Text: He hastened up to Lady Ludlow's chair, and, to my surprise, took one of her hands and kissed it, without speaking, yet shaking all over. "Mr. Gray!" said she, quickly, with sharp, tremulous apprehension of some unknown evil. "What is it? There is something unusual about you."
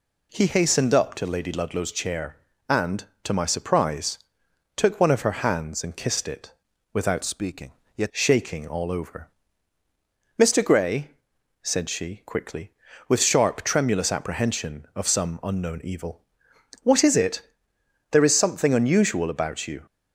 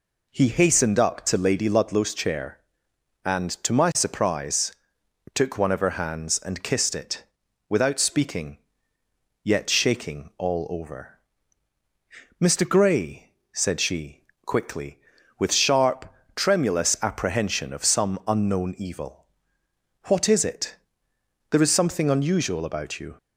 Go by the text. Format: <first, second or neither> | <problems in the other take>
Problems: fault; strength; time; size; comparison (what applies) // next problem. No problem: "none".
second | changes voice from "speaking" to "yet"; from 7.2 to 8.1 s; 0.9 s long